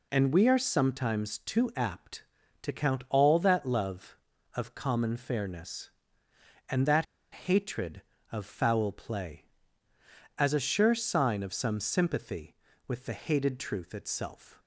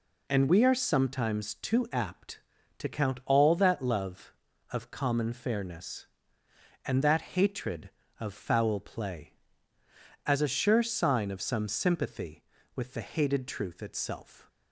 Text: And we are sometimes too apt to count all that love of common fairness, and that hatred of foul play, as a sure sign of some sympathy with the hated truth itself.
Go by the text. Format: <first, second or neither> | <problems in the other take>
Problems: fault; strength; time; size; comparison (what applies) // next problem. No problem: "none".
second | pauses between "that" and "hatred"; slight; at 7.0 s; 0.27 s long